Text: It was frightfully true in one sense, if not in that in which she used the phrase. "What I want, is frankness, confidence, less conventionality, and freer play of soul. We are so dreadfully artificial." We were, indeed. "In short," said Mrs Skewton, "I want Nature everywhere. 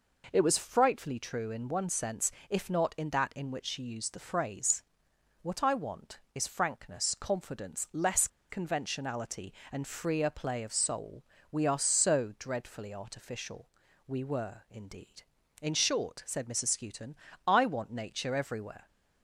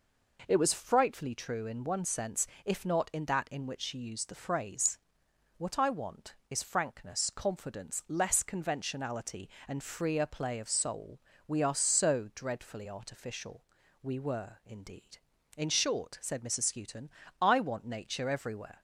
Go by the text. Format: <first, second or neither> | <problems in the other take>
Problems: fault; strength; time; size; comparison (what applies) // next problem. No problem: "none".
second | pauses between "less" and "conventionality"; slight; at 8.2 s; 0.22 s long